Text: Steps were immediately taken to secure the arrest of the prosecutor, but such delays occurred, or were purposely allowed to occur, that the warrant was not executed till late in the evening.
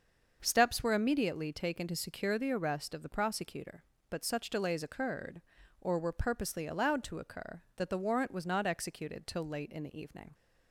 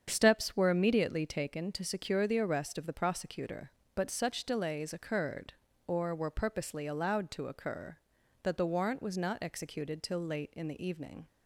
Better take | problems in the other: neither | starts louder than the rest; the same in both

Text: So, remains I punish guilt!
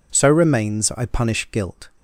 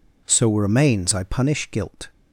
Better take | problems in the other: neither | none

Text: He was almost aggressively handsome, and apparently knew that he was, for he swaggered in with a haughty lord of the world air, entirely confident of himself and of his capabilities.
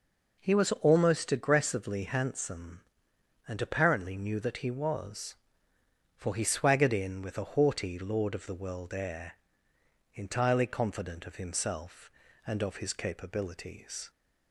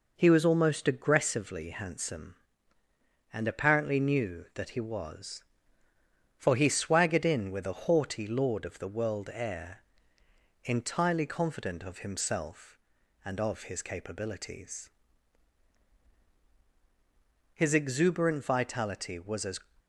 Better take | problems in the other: first | goes on to say "His exuberant vitality was as"; strong; from 17.5 s on; 2.0 s long

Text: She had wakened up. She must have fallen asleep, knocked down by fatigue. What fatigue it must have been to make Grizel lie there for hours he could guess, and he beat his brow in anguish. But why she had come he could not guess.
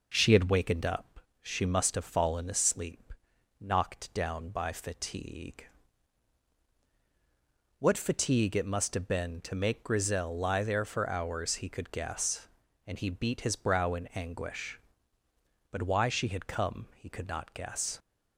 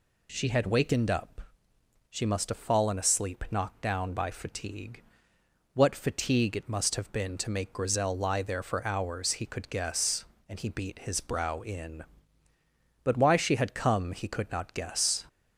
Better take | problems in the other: first | skips "anguish"; at 12.5 s

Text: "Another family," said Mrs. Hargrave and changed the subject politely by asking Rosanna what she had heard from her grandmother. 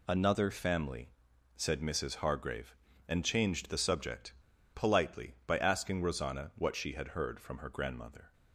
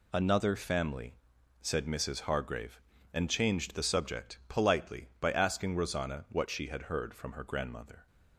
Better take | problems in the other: second | pauses between "subject" and "politely"; at 4.3 s; 0.41 s long

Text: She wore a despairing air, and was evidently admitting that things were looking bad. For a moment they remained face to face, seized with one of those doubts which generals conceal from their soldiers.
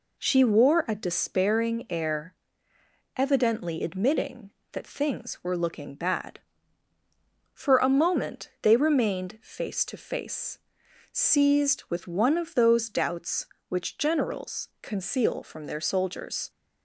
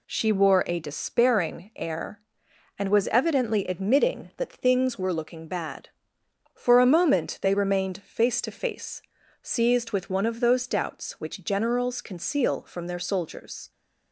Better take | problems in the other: second | skips "and was"; at 2.7 s

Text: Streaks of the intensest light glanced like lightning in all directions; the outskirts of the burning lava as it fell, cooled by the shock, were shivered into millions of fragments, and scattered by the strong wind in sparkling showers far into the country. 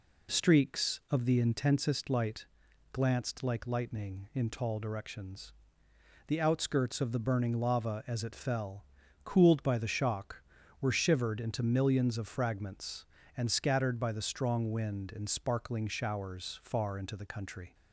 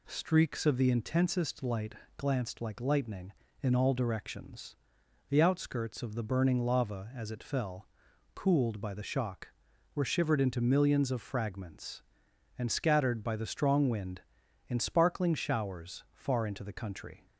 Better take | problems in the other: second | pauses between "light" and "glanced"; noticeable; at 2.4 s; 0.46 s long; slight in the second // says "tall" for "all"; at 4.4 s

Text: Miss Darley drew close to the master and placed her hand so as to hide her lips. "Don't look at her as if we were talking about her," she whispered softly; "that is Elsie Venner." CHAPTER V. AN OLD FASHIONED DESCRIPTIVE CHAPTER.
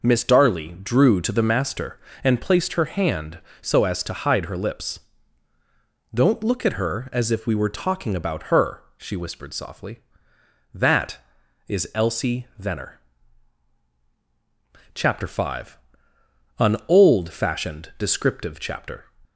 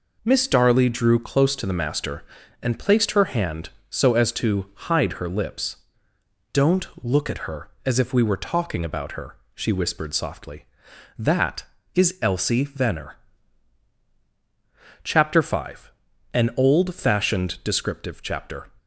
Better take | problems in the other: second | skips "close"; at 1.2 s

